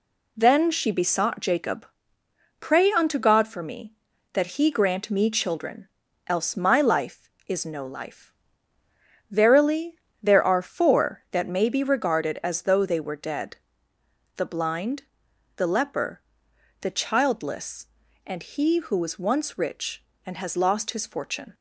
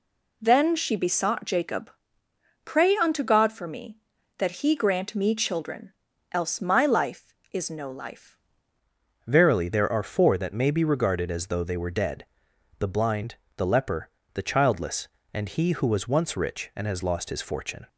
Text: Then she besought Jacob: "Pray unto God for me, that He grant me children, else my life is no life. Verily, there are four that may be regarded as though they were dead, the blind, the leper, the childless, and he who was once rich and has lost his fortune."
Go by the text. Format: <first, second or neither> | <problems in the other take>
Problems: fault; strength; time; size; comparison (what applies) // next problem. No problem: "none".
first | changes voice at "Verily"; from 9.2 s on; 8.6 s long